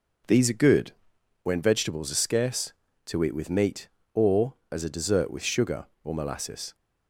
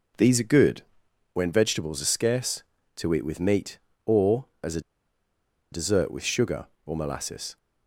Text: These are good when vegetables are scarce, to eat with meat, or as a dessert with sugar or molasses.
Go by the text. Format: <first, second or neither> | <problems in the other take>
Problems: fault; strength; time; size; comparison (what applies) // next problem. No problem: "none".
first | pauses between "good" and "when"; noticeable; at 0.8 s; 0.50 s long; noticeable in the first // pauses between "a" and "dessert"; noticeable; at 4.7 s; 0.91 s long